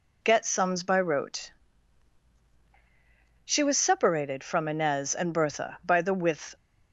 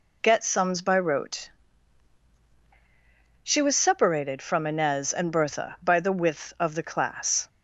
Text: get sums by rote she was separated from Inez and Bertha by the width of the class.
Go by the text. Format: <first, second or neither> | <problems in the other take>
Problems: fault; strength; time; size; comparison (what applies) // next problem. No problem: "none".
second | pauses between "rote" and "she"; strong; at 1.4 s; 1.9 s long; strong in the second // stops before "of the class"; at 6.5 s